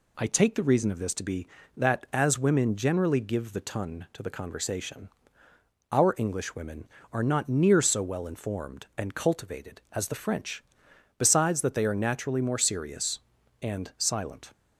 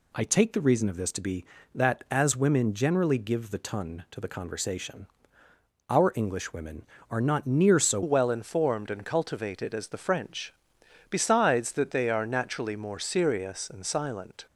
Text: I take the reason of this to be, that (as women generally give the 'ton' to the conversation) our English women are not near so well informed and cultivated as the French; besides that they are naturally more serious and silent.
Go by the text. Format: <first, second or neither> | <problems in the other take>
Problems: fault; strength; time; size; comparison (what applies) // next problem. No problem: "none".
first | changes voice at "well"; from 8.0 s on; 6.4 s long